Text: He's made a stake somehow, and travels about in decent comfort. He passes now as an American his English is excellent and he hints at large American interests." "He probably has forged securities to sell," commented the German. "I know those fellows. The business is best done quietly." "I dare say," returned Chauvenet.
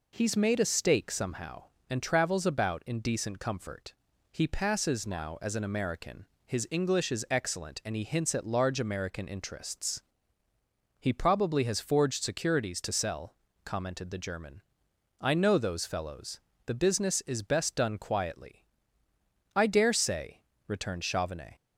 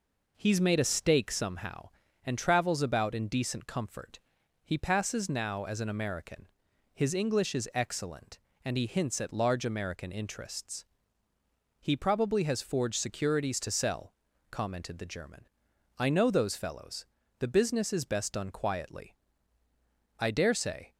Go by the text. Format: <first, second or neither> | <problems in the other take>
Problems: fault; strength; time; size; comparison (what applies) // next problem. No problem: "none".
first | pauses between "American" and "his"; noticeable; at 6.4 s; 0.46 s long; slight in the first // stops before "returned Chauvenet"; at 20.9 s